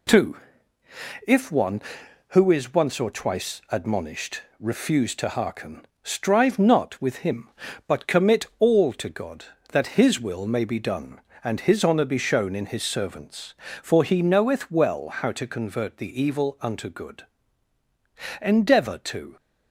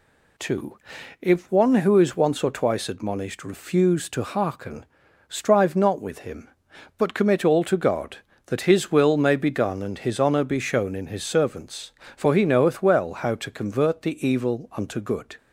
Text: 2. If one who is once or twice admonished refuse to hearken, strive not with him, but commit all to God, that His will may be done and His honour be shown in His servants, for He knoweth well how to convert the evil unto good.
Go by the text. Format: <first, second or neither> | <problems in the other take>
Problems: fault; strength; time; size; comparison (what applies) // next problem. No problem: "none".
second | pauses between "admonished" and "refuse"; slight; at 4.3 s; 0.18 s long // goes on to say "Endeavour to"; noticeable; from 18.3 s on; 0.96 s long